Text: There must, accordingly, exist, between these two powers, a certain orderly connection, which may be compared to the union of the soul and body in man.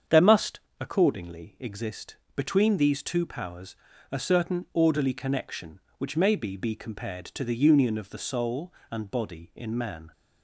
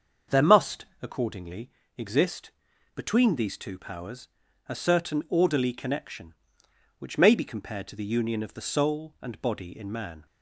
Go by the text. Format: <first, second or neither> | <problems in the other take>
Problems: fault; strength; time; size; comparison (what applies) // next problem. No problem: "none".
second | starts louder than the rest; strong; until 1.3 s; 7.5 dB; also in the second // says "be" twice; at 6.5 s